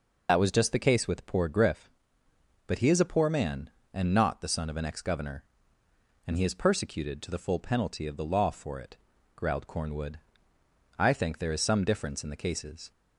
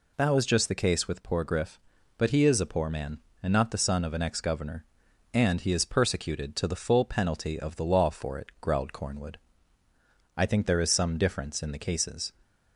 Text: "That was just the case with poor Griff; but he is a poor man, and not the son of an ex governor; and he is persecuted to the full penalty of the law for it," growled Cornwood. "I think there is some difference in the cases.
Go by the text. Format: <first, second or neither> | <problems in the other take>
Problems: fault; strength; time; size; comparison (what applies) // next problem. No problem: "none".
second | loses the start of "That"; at 0.2 s; 75 ms